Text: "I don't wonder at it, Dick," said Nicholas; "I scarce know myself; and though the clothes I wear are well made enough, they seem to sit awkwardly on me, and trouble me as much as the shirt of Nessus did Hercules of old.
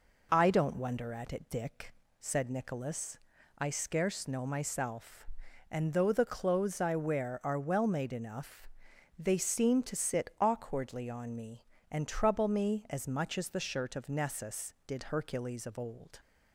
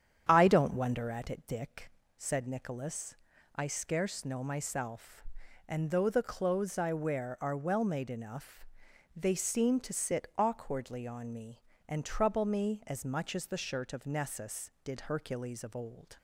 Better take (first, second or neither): first